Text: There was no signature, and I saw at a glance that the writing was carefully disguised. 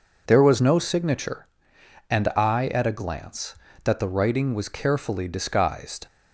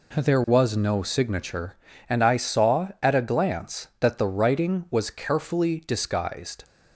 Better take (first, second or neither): second